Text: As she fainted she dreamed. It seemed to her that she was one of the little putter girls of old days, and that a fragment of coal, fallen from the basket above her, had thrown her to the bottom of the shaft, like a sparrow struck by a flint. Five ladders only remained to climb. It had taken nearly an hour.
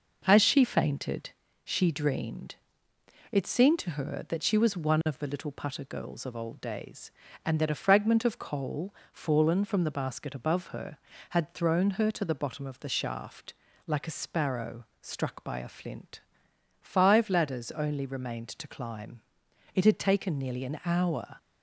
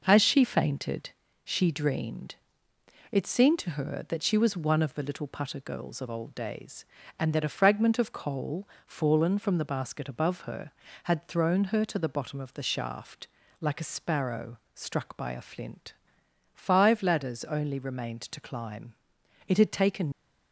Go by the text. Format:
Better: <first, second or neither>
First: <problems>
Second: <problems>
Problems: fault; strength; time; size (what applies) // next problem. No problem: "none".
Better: first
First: pauses between "fainted" and "she"; slight; at 1.3 s; 0.34 s long // pauses between "sparrow" and "struck"; slight; at 14.8 s; 0.16 s long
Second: pauses between "fainted" and "she"; slight; at 1.1 s; 0.34 s long // pauses between "sparrow" and "struck"; slight; at 14.5 s; 0.16 s long // stops before "nearly an hour"; at 20.1 s